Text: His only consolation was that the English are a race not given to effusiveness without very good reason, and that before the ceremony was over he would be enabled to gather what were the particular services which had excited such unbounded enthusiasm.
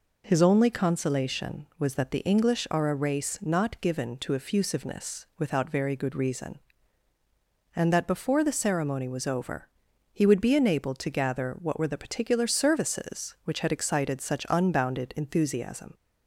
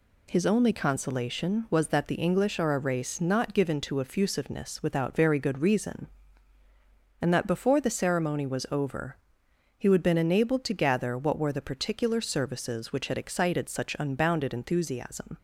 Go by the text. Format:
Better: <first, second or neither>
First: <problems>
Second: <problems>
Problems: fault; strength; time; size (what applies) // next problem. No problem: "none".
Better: first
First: pauses between "over" and "he"; noticeable; at 9.6 s; 0.46 s long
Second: pauses between "over" and "he"; noticeable; at 9.1 s; 0.64 s long // says "been" for "be"; at 10.0 s